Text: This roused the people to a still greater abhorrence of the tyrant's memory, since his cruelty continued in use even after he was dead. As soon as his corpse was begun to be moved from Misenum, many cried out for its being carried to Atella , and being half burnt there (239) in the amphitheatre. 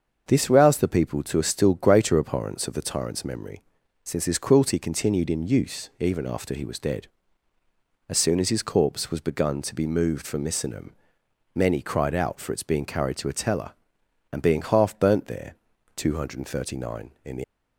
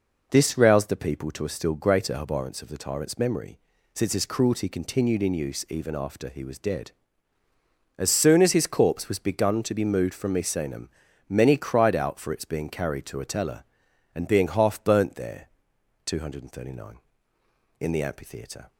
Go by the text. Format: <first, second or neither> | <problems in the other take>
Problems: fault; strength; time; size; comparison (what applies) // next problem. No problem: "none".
second | starts louder than the rest; until 1.2 s; 6.5 dB // stops before "amphitheatre"; at 17.4 s